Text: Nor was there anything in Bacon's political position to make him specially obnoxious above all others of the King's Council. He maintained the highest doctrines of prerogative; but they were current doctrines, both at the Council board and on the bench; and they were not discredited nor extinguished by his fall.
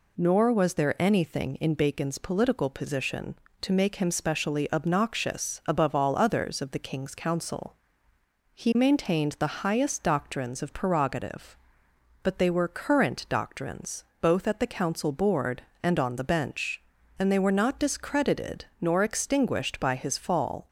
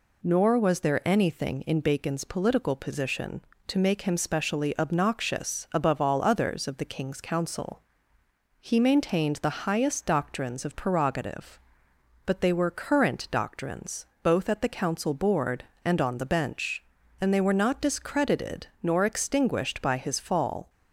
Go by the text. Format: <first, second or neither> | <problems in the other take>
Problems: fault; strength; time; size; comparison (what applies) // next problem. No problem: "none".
neither | pauses between "discredited" and "nor"; slight; the same in both